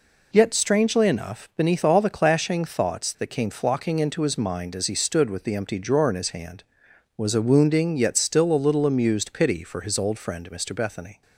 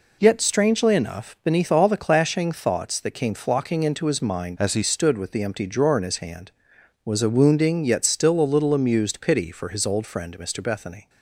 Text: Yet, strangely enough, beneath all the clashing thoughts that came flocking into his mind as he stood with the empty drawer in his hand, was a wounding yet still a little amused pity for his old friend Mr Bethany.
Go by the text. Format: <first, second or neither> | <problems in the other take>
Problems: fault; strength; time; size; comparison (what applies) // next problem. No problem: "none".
first | changes voice from "as" to "he"; from 4.5 to 4.8 s; 0.3 s long